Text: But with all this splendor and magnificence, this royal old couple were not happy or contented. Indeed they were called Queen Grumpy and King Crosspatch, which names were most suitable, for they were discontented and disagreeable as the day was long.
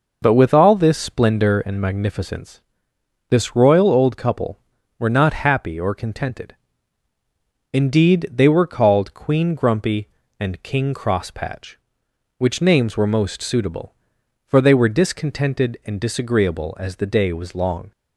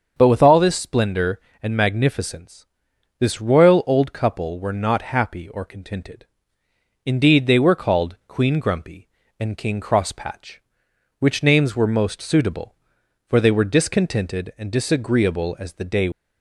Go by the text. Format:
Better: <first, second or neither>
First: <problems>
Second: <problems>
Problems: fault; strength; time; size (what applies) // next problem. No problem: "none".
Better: first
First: none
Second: starts louder than the rest; until 1.1 s; 6.5 dB // stops before "was long"; at 16.1 s